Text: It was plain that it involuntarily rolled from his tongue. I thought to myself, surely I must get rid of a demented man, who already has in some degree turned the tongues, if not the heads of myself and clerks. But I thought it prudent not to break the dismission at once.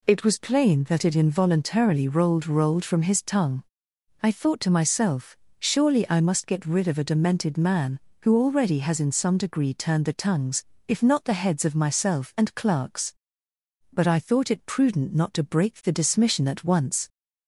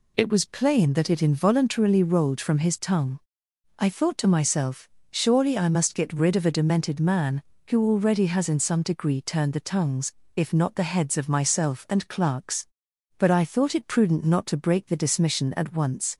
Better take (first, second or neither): second